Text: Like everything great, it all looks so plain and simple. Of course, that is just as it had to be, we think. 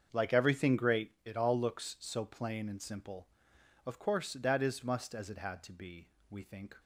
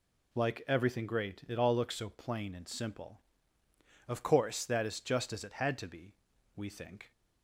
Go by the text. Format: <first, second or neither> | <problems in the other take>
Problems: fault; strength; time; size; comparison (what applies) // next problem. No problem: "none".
second | starts louder than the rest; until 1.1 s; 7 dB // says "must" for "just"; at 4.8 s